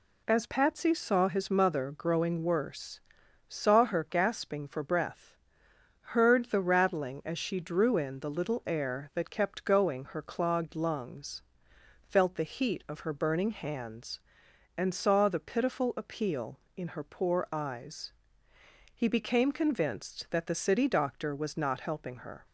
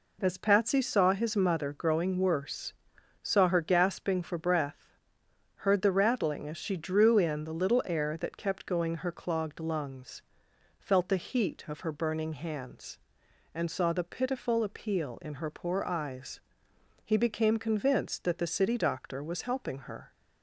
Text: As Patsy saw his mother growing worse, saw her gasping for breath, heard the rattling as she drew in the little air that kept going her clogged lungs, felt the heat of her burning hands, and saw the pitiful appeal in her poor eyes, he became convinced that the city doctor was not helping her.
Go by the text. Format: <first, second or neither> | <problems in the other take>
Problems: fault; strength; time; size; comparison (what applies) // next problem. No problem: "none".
first | skips "not"; at 19.4 s